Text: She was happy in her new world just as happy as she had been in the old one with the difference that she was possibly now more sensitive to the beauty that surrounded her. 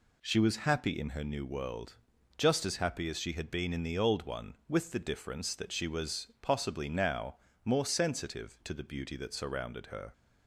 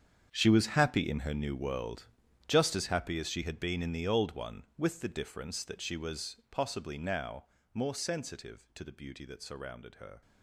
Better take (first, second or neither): first